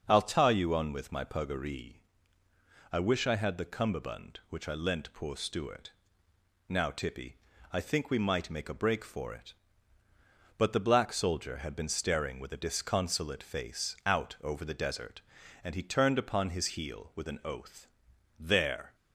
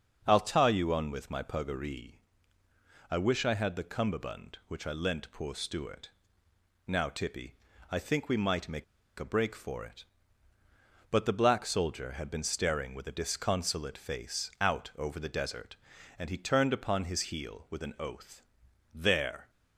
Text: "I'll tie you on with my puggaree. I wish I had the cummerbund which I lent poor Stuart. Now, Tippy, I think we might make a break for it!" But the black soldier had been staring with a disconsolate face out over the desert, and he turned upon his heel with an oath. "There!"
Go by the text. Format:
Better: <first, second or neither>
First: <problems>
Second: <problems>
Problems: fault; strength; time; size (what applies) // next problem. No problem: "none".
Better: first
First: starts louder than the rest; until 1.0 s; 6.5 dB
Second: starts louder than the rest; until 1.2 s; 6.5 dB // pauses between "make" and "a"; slight; at 8.8 s; 0.35 s long